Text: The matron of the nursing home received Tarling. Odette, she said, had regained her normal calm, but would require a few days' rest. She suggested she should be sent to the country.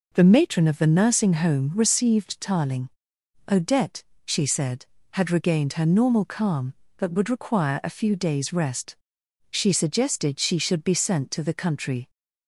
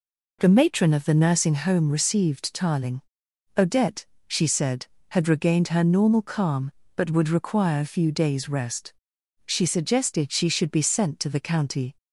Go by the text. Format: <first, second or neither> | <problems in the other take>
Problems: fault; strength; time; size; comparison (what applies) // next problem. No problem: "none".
first | says "county" for "country"; at 11.4 s